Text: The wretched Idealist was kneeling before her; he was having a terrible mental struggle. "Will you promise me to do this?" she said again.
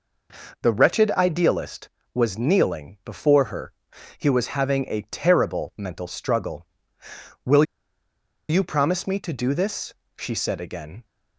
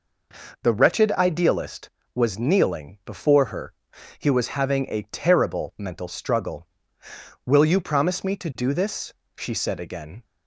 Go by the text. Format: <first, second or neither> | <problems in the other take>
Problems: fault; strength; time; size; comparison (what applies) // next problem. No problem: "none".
second | pauses between "Will" and "you"; noticeable; at 7.6 s; 0.84 s long